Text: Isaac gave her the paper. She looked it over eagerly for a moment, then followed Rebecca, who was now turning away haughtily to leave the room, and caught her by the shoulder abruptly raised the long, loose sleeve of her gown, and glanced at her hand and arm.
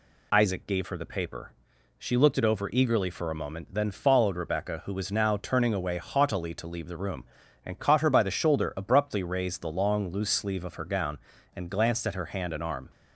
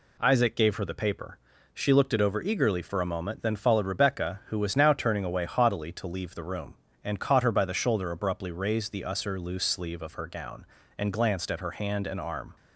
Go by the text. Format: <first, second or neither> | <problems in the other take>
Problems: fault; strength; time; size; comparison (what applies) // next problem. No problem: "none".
first | says "usser" for "long"; at 9.0 s